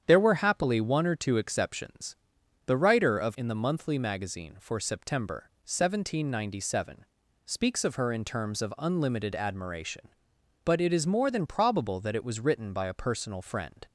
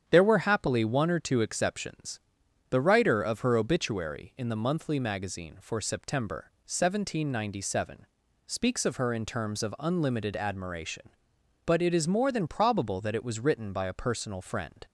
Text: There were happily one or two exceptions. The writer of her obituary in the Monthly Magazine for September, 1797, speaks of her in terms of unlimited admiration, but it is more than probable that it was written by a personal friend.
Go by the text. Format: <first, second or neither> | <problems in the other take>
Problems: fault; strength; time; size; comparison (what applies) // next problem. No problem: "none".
second | starts louder than the rest; strong; until 1.0 s; 8.5 dB; strong in the second // skips "her obituary"; at 3.3 s